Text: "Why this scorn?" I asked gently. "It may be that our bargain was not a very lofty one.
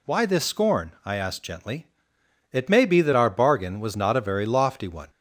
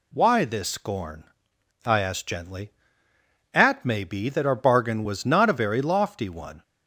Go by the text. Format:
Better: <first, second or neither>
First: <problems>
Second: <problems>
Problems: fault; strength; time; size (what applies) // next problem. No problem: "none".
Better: first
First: none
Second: says "At" for "It"; at 3.5 s